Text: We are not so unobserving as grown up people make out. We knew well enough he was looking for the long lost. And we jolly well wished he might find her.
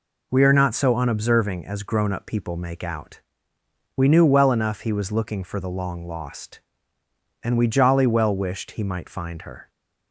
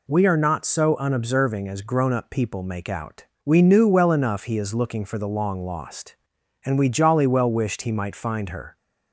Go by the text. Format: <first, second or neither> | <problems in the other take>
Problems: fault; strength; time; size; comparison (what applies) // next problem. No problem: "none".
first | says "is" for "was"; at 4.5 s